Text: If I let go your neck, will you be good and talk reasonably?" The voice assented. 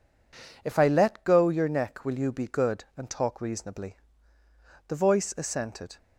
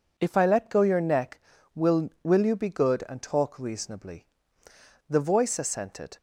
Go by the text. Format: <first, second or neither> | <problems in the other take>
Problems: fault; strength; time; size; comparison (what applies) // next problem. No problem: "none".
first | says "will" twice; at 2.2 s